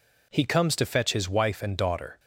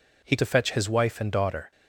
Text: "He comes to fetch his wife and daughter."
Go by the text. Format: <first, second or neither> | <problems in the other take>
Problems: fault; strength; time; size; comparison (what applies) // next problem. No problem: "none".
first | skips "comes"; at 0.3 s